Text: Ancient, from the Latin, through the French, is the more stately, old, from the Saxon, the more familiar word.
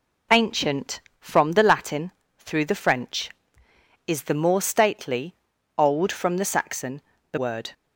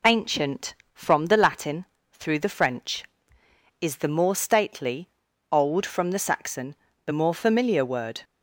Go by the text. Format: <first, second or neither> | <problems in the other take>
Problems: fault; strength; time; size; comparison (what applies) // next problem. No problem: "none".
second | skips "more familiar"; at 7.3 s